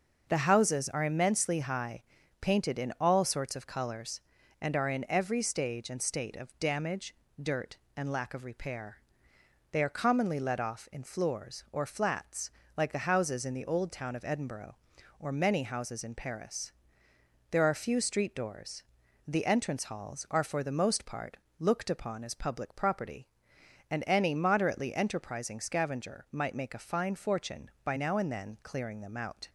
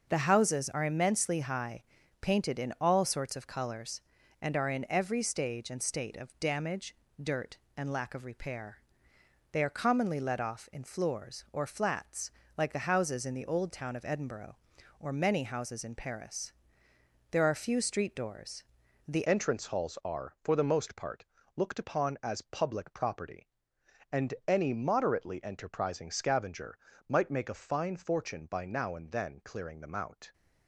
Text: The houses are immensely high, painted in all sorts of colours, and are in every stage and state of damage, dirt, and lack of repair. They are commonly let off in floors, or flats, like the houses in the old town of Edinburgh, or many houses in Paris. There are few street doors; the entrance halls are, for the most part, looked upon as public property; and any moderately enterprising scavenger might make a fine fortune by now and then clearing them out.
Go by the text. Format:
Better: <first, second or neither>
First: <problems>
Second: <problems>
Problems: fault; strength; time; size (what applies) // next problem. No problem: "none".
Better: first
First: starts louder than the rest; noticeable; until 1.2 s; 6 dB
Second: starts louder than the rest; noticeable; until 1.1 s; 6 dB // changes voice at "entrance"; from 19.2 s on; 11.1 s long // pauses between "scavenger" and "might"; slight; at 26.7 s; 0.32 s long